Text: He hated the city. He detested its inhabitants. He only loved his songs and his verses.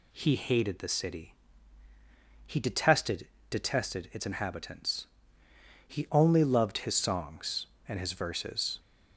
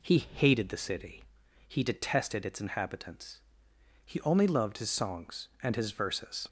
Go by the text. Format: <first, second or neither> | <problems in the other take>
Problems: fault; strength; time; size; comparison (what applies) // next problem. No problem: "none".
second | says "detested" twice; at 3.4 s